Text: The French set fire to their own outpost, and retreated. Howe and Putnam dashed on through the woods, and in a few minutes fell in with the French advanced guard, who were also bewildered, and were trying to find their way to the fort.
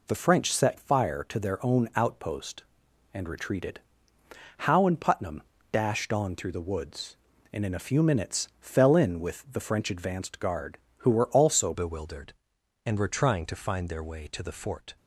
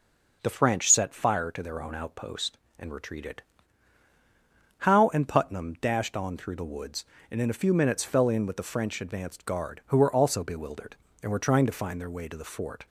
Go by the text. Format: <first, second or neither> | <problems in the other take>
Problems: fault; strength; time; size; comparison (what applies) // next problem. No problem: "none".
second | pauses between "Putnam" and "dashed"; slight; at 5.4 s; 0.30 s long // changes voice at "bewildered"; from 11.7 s on; 3.2 s long